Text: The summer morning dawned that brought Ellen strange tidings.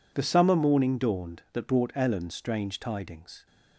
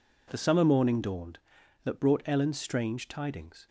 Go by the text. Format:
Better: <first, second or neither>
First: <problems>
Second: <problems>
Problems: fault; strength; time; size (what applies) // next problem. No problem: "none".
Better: neither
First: none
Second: none